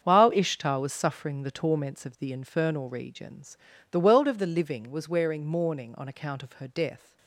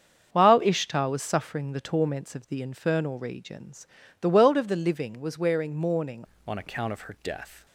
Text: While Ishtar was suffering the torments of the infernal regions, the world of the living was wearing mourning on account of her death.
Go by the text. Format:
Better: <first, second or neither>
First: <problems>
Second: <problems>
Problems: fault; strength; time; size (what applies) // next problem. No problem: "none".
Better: first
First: starts louder than the rest; strong; until 1.0 s; 7.5 dB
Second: starts louder than the rest; strong; until 1.3 s; 7 dB // changes voice at "on"; from 6.4 s on; 1.2 s long